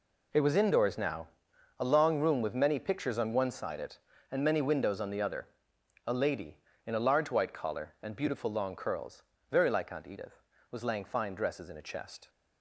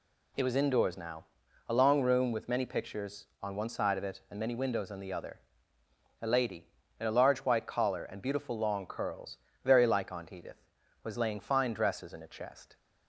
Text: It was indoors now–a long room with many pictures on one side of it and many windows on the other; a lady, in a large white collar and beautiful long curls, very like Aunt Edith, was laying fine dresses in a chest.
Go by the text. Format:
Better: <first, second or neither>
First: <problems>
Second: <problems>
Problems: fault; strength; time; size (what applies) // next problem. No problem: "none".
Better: second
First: skips "of"; at 3.8 s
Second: none